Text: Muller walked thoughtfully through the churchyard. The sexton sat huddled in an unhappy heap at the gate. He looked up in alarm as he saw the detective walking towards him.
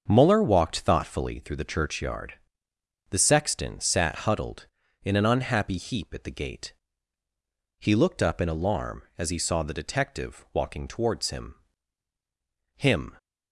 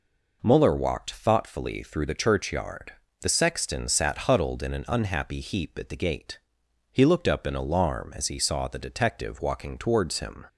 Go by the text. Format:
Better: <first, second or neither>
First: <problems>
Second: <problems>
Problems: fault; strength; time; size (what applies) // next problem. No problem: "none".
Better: second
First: starts louder than the rest; until 1.0 s; 7 dB // says "him" twice; at 12.7 s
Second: none